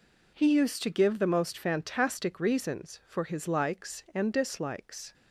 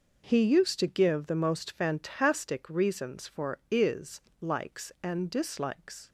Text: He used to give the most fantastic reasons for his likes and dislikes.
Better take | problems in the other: first | says "is" for "his"; at 3.6 s

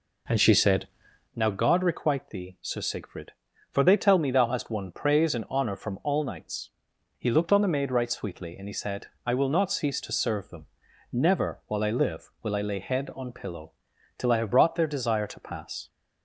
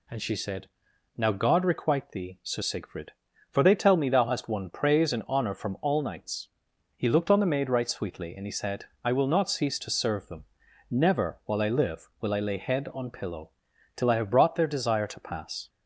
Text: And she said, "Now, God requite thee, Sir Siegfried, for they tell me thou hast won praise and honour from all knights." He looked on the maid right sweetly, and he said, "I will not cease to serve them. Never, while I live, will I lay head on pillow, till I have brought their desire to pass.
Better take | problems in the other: second | starts louder than the rest; noticeable; until 1.4 s; 4 dB

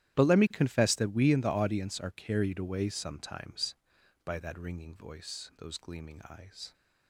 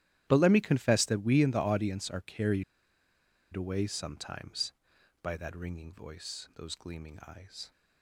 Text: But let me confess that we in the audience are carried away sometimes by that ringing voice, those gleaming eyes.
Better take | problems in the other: first | starts louder than the rest; strong; until 1.2 s; 12.5 dB; strong in the first // pauses between "carried" and "away"; noticeable; at 2.6 s; 0.90 s long

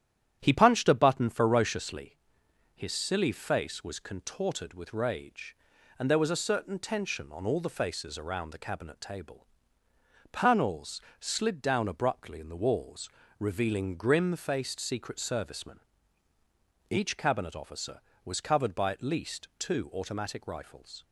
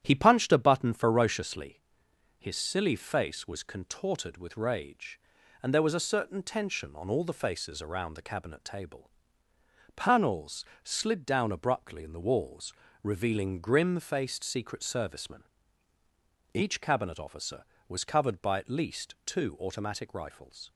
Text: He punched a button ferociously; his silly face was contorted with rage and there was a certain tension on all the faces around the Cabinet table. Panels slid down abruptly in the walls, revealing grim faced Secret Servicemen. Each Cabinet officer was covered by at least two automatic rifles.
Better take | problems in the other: neither | starts louder than the rest; strong; the same in both // pauses between "Panels" and "slid"; slight; the same in both

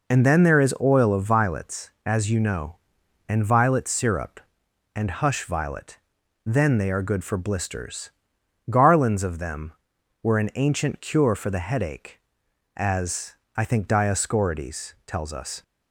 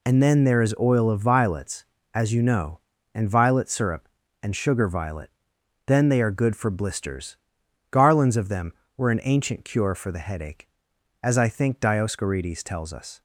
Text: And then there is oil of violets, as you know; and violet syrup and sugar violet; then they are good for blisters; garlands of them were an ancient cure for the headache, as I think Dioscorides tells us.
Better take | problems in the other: second | says "hush" for "sugar"; at 5.0 s // pauses between "as" and "I"; slight; at 13.3 s; 0.24 s long

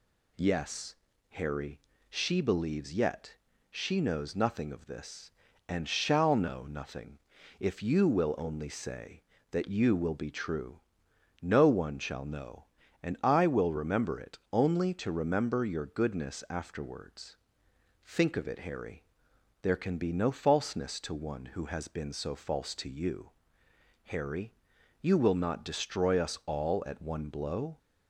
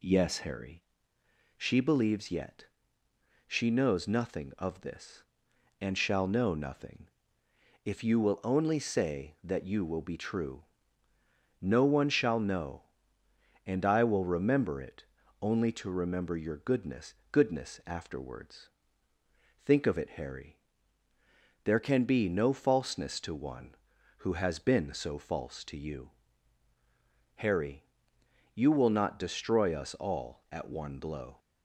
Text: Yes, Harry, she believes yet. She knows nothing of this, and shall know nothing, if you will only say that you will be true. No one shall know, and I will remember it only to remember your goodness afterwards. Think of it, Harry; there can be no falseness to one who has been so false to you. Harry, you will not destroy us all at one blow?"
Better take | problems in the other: first | pauses between "it" and "only"; slight; at 15.0 s; 0.36 s long // says "goodness" twice; at 17.3 s

